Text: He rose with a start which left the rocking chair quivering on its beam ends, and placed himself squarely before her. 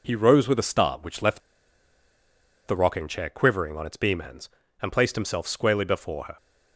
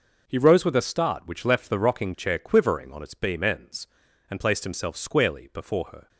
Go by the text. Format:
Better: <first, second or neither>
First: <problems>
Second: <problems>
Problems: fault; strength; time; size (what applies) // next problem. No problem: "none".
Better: second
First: pauses between "left" and "the"; strong; at 1.4 s; 1.2 s long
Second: none